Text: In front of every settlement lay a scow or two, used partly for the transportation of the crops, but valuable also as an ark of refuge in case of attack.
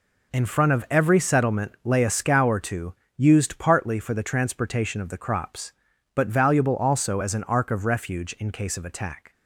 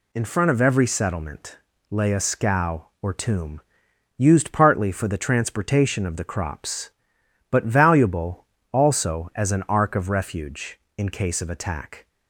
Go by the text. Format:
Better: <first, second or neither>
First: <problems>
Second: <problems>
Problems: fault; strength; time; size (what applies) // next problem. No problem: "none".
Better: first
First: none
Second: pauses between "settlement" and "lay"; slight; at 1.5 s; 0.32 s long // says "tomb" for "two"; at 3.1 s // pauses between "valuable" and "also"; slight; at 8.4 s; 0.26 s long